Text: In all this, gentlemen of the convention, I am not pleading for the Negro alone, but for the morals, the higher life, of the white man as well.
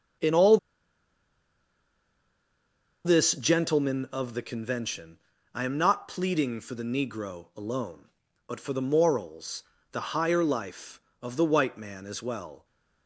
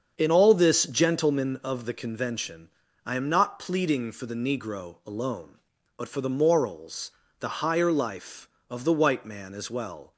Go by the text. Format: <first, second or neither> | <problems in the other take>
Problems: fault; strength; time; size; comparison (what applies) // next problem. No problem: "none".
second | starts louder than the rest; until 3.6 s; 7 dB; also in the second // pauses between "all" and "this"; strong; at 0.5 s; 2.4 s long